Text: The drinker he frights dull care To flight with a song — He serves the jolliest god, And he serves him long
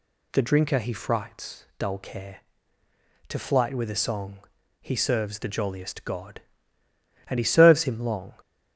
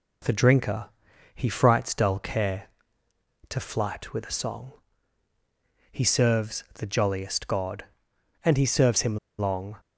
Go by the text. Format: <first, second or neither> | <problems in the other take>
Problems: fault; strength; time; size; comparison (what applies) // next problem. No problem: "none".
first | pauses between "drinker" and "he"; noticeable; at 0.8 s; 0.48 s long // pauses between "him" and "long"; slight; at 9.1 s; 0.21 s long